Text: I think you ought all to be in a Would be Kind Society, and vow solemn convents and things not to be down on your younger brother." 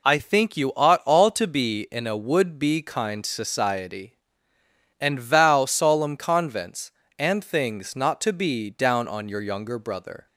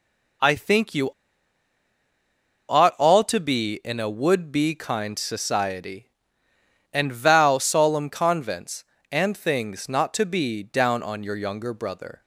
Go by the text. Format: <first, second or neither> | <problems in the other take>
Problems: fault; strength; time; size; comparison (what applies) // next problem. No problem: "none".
first | pauses between "you" and "ought"; strong; at 1.0 s; 1.5 s long